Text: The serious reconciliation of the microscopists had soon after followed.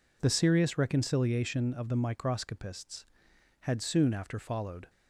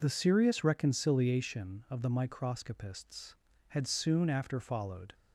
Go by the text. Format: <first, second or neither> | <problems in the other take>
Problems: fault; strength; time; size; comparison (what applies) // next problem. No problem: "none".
neither | none